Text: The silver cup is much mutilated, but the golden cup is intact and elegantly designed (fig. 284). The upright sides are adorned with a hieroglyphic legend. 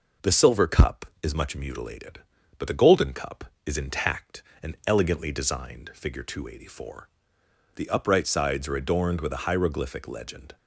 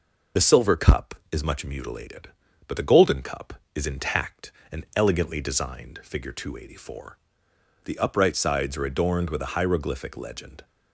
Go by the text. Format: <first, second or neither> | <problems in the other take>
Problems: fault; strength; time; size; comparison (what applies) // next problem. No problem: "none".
first | loses the start of "The"; at 0.3 s; 45 ms